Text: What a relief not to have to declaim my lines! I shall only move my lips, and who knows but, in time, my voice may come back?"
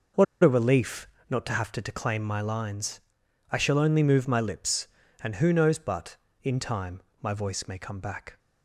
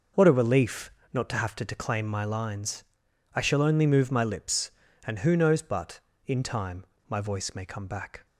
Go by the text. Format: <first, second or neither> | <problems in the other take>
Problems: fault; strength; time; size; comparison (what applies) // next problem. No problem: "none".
second | pauses between "What" and "a"; slight; at 0.2 s; 0.18 s long // pauses between "relief" and "not"; slight; at 1.0 s; 0.20 s long; slight in the second